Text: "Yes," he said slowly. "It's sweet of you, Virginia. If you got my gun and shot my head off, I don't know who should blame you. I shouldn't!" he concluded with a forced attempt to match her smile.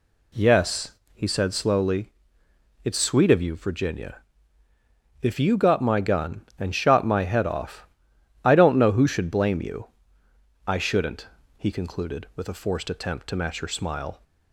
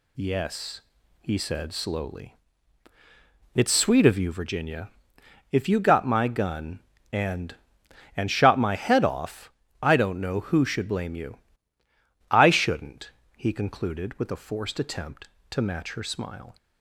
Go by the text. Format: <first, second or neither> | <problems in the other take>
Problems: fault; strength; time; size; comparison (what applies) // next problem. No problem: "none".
first | says "and" twice; at 8.1 s